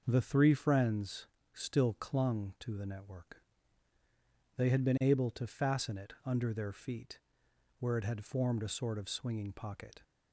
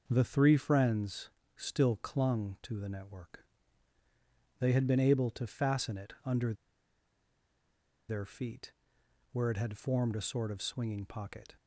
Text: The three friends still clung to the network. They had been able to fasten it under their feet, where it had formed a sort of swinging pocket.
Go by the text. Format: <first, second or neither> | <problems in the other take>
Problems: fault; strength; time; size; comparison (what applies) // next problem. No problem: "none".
first | pauses between "friends" and "still"; slight; at 1.2 s; 0.26 s long; slight in the first // pauses between "under" and "their"; strong; at 6.5 s; 1.5 s long